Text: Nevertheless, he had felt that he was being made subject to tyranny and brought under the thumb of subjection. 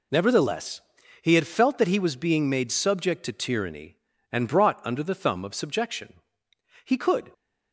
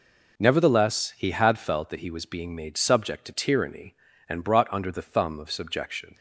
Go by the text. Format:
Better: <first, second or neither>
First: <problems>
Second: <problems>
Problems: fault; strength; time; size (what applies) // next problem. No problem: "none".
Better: second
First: goes on to say "He could"; slight; from 6.8 s on; 0.47 s long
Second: none